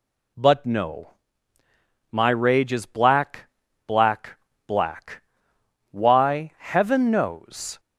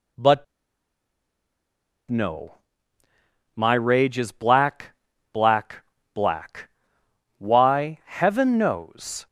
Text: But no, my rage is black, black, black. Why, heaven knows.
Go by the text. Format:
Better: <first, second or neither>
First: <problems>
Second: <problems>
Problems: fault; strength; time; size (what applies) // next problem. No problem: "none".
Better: first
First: none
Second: pauses between "But" and "no"; strong; at 0.4 s; 1.6 s long